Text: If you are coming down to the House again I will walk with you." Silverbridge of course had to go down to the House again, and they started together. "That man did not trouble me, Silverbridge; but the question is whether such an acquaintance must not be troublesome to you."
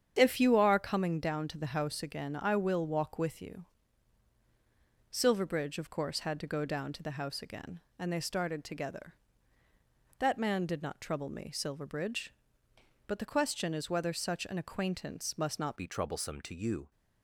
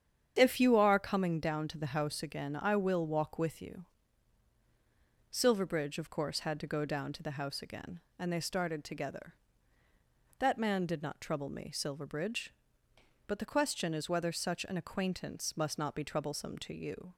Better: second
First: starts louder than the rest; strong; until 1.1 s; 8.5 dB // changes voice at "be"; from 15.7 s on; 1.2 s long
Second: starts louder than the rest; strong; until 1.3 s; 8.5 dB

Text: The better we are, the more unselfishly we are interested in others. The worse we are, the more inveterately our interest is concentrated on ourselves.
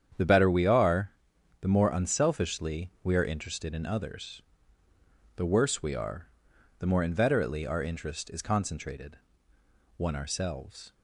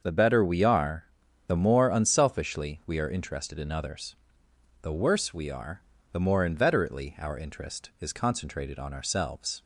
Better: second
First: starts louder than the rest; strong; until 1.6 s; 8.5 dB // says "one" for "on"; at 9.9 s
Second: starts louder than the rest; until 1.0 s; 6.5 dB

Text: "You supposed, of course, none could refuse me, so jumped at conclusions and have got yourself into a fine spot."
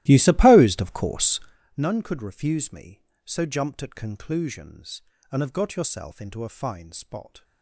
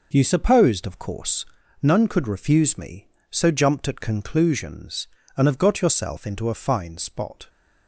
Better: second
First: starts louder than the rest; strong; until 1.7 s; 16 dB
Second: none

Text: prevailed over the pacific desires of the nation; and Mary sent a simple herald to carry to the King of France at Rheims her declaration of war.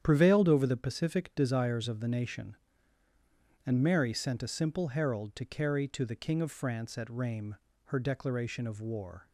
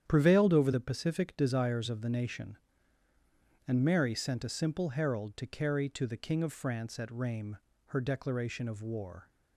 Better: neither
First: starts louder than the rest; strong; until 1.0 s; 9 dB // pauses between "Rheims" and "her"; slight; at 7.5 s; 0.32 s long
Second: starts louder than the rest; strong; until 1.0 s; 9.5 dB // pauses between "Rheims" and "her"; slight; at 7.5 s; 0.32 s long

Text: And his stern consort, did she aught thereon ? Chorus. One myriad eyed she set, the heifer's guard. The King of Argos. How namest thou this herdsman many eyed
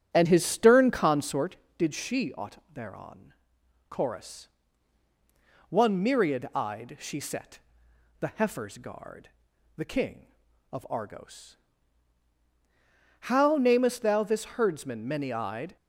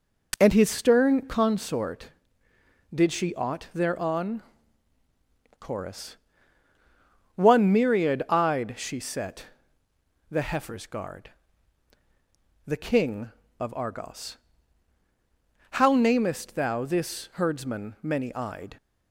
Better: second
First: starts louder than the rest; strong; until 1.5 s; 8 dB // pauses between "aught" and "thereon"; slight; at 2.5 s; 0.16 s long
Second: none

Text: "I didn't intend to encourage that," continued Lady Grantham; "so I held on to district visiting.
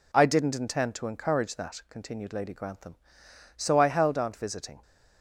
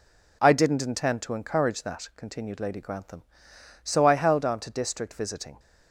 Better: second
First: skips "to district"; at 4.3 s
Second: none

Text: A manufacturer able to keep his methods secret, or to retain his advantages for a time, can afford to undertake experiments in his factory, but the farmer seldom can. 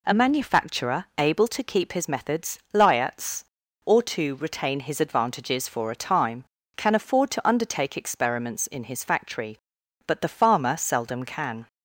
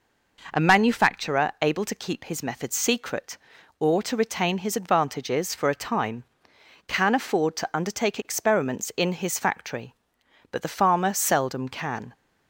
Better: second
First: says "liats" for "secret"; at 2.7 s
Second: none

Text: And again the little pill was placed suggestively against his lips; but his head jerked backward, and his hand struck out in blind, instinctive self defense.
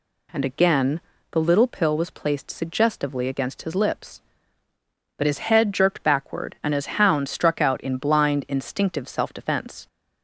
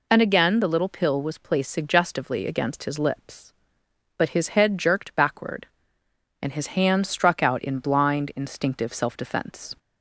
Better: second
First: pauses between "again" and "the"; slight; at 0.9 s; 0.32 s long // says "hound" for "hand"; at 7.0 s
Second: none

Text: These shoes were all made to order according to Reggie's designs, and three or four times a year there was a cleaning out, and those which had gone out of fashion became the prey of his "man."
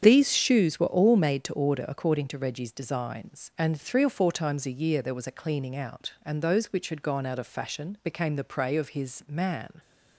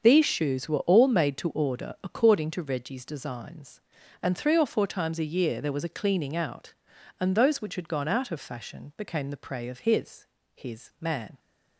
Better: first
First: starts louder than the rest; strong; until 1.0 s; 8 dB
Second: starts louder than the rest; until 1.0 s; 7 dB // says "his" twice; at 10.5 s

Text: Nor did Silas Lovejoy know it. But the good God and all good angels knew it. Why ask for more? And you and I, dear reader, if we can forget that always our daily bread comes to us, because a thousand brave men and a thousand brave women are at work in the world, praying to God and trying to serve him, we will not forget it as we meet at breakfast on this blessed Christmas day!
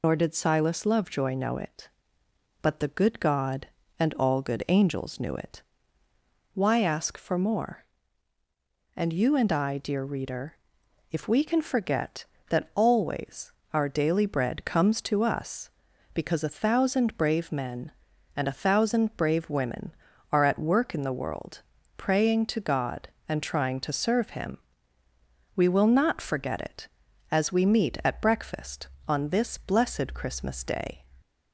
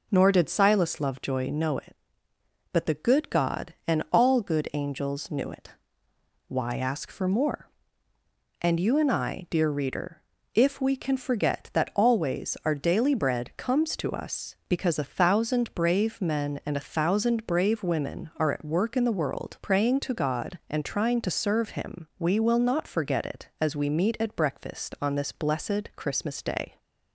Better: second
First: loses the start of "Nor"; at 0.0 s; 70 ms // pauses between "always" and "our"; slight; at 13.5 s; 0.22 s long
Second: none

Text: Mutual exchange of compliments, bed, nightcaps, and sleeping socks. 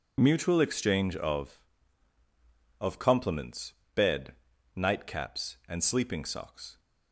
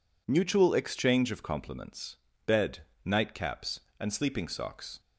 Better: second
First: says "of" twice; at 2.8 s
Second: none

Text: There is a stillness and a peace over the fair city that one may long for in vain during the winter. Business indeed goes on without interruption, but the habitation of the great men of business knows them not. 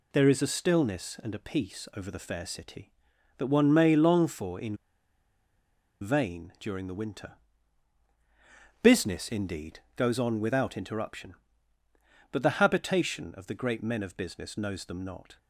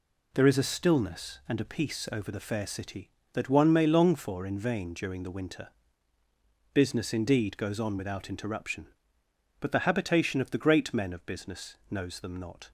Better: second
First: pauses between "in" and "vain"; strong; at 4.7 s; 1.2 s long // pauses between "indeed" and "goes"; slight; at 9.7 s; 0.16 s long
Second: none

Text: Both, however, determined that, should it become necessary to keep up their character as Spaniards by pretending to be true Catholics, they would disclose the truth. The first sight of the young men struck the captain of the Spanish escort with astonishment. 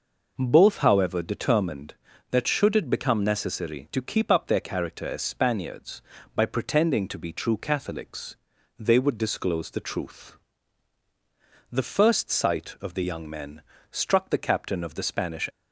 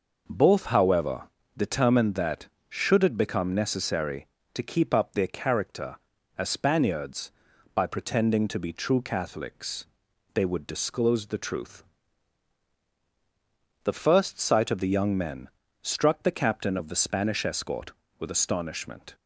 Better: second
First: pauses between "men" and "struck"; slight; at 13.6 s; 0.30 s long // stops before "escort with astonishment"; at 15.5 s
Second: pauses between "men" and "struck"; slight; at 15.4 s; 0.34 s long

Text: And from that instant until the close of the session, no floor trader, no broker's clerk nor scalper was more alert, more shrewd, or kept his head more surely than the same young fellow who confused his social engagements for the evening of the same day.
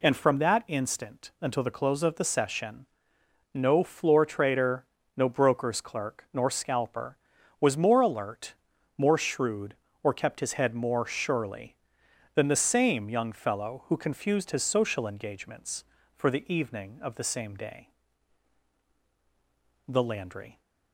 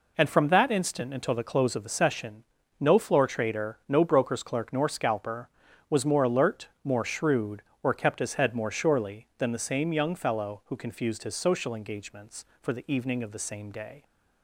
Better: second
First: goes on to say "The Landry"; noticeable; from 19.8 s on; 0.74 s long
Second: none

